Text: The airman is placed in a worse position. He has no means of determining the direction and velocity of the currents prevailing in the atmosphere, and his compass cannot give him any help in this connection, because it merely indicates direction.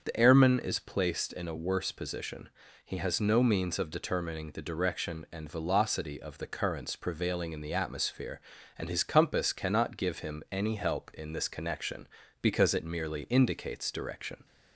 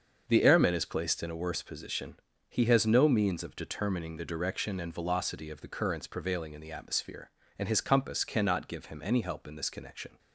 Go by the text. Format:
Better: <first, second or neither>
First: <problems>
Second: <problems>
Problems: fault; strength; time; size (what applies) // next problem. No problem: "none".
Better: first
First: starts louder than the rest; until 1.0 s; 7 dB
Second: starts louder than the rest; until 1.2 s; 6.5 dB // stops before "because it merely indicates direction"; at 10.1 s